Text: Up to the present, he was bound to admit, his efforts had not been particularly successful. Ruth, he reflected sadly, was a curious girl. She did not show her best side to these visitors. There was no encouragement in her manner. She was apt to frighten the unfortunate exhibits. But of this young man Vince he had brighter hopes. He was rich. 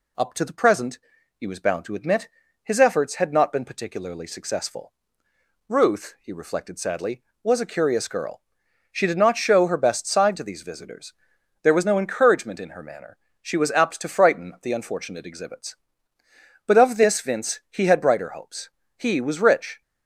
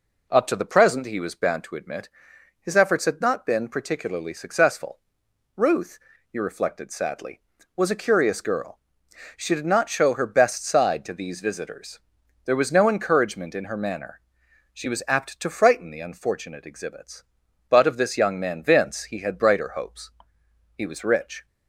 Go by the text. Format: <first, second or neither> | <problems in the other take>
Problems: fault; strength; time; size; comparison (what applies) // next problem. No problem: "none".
second | skips "young man"; at 17.2 s